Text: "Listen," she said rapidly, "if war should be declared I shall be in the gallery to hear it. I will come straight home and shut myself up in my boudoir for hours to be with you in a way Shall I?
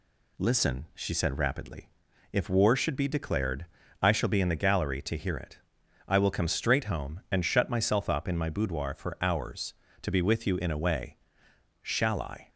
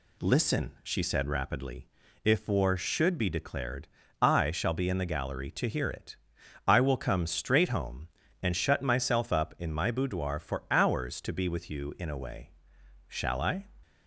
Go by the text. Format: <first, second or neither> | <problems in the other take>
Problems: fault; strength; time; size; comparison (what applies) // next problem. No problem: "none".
neither | pauses between "declared" and "I"; slight; the same in both // pauses between "way" and "Shall"; noticeable; the same in both